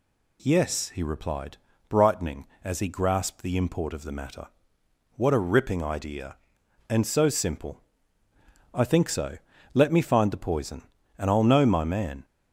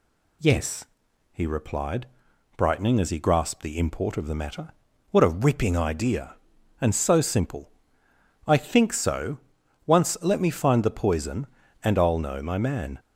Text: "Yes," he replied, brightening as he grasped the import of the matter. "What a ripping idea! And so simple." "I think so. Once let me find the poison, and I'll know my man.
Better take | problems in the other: second | skips "Once"; at 9.5 s

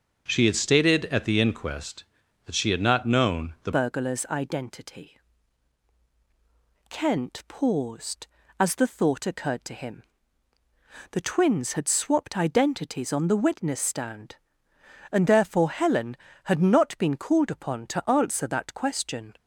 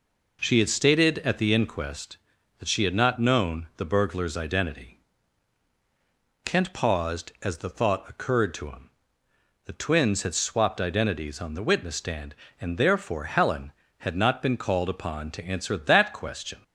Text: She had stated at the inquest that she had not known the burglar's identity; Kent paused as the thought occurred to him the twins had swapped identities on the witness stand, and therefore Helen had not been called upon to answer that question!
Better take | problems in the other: second | starts louder than the rest; until 1.2 s; 6 dB // changes voice at "burglar's"; from 3.7 s on; 15.6 s long // pauses between "him" and "the"; at 10.0 s; 1.0 s long; noticeable in the second

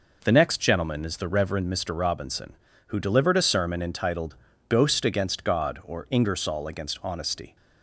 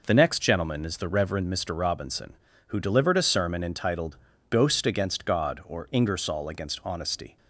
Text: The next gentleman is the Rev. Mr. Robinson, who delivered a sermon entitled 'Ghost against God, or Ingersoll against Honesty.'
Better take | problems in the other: neither | pauses between "entitled" and "Ghost"; slight; the same in both

